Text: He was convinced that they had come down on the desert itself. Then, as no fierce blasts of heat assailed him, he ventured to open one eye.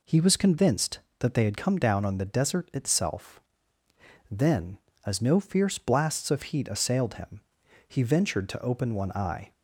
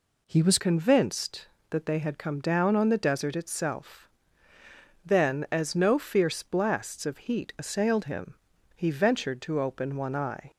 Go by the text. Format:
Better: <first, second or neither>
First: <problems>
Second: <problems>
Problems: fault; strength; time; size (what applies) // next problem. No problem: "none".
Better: first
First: none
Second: changes voice at "convinced"; from 0.5 s on; 10.0 s long